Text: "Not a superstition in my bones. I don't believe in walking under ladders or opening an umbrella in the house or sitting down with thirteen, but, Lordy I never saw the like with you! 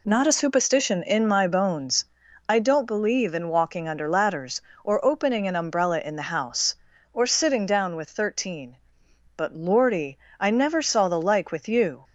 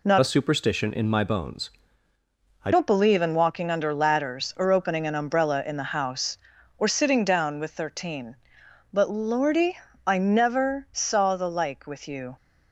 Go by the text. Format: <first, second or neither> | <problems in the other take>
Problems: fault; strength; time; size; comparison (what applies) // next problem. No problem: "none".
first | changes voice from "a" to "I"; from 0.2 to 2.7 s; 2.5 s long // pauses between "Lordy" and "I"; slight; at 9.7 s; 0.26 s long; slight in the first